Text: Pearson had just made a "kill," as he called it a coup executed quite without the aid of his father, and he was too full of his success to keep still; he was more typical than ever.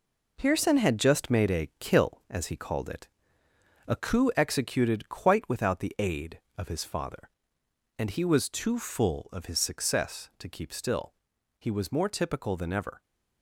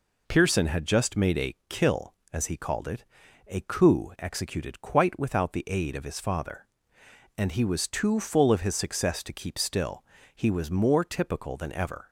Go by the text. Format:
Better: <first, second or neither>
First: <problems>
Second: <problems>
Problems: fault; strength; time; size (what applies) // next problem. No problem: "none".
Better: second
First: gets quieter; throughout; 7 dB // pauses between "it" and "a"; noticeable; at 3.0 s; 0.80 s long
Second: pauses between "it" and "a"; at 3.0 s; 0.44 s long